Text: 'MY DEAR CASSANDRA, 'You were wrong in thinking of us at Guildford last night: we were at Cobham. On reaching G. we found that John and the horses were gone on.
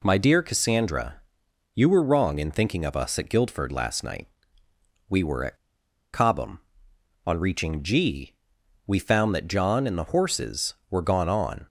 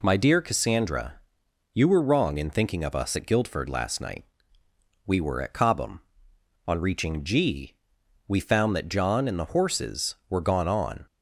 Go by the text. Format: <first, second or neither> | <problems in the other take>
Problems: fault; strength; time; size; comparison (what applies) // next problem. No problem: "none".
second | pauses between "at" and "Cobham"; noticeable; at 5.5 s; 0.58 s long